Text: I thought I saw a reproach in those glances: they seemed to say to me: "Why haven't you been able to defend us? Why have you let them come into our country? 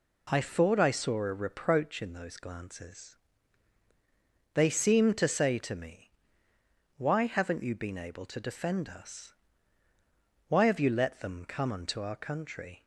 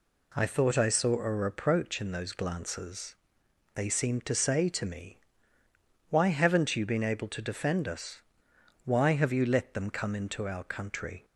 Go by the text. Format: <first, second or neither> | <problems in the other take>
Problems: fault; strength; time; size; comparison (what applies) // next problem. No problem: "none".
second | says "unto" for "into"; at 11.7 s